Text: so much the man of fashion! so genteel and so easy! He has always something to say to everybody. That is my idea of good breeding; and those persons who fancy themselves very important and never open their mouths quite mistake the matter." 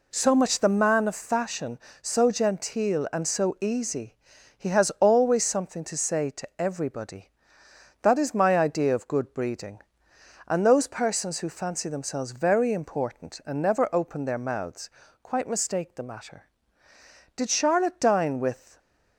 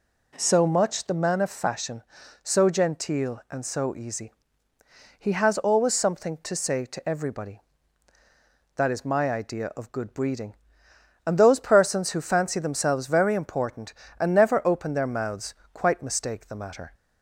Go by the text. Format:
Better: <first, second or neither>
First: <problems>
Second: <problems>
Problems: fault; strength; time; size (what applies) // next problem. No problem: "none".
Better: second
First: pauses between "mouths" and "quite"; slight; at 14.8 s; 0.32 s long // goes on to say "Did Charlotte dine with"; from 17.3 s on; 1.4 s long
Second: pauses between "mouths" and "quite"; slight; at 15.5 s; 0.18 s long